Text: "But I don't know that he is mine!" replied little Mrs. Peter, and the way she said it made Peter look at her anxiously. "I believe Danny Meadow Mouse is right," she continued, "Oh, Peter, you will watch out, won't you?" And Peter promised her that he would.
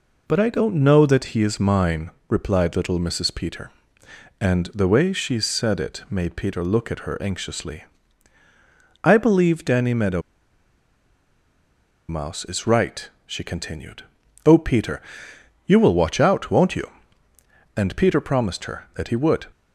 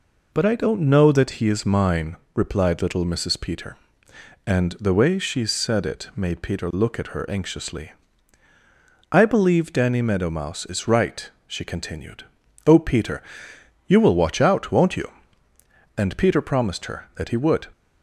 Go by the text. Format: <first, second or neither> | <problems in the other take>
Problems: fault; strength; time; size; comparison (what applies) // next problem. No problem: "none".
second | pauses between "Meadow" and "Mouse"; strong; at 10.2 s; 1.8 s long